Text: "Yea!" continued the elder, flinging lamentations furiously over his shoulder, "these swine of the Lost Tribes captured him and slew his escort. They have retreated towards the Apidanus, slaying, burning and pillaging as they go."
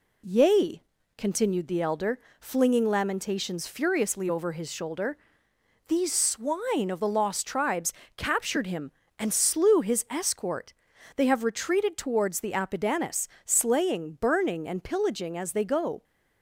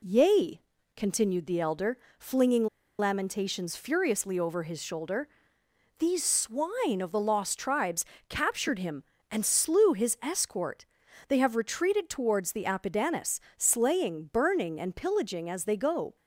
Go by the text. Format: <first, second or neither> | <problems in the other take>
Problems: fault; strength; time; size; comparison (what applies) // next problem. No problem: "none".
first | pauses between "flinging" and "lamentations"; slight; at 2.6 s; 0.31 s long // pauses between "Tribes" and "captured"; slight; at 8.0 s; 0.26 s long; slight in the first